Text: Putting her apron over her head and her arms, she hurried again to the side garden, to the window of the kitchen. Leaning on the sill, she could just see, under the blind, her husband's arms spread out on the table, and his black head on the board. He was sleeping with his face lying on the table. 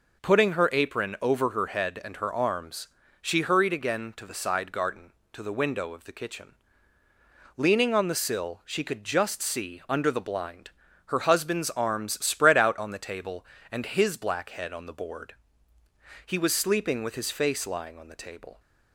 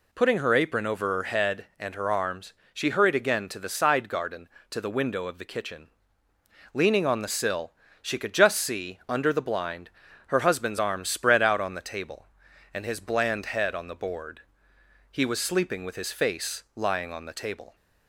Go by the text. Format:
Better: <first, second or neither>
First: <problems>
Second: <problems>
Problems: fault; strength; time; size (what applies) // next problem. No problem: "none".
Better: first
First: none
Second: says "bland" for "black"; at 12.9 s